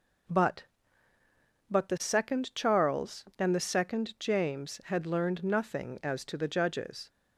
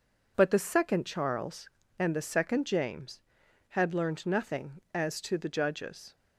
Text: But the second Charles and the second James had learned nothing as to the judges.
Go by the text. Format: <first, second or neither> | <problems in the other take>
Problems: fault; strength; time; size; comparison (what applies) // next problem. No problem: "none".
second | says "But" twice; at 1.7 s